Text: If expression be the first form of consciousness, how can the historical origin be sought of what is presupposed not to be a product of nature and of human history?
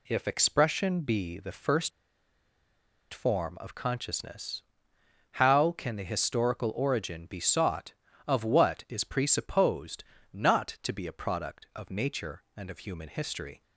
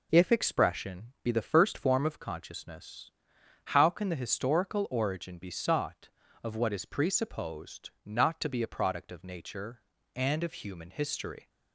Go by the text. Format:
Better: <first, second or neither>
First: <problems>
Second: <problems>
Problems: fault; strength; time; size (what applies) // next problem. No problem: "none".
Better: second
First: pauses between "first" and "form"; at 1.9 s; 1.2 s long // pauses between "presupposed" and "not"; slight; at 10.0 s; 0.28 s long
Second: none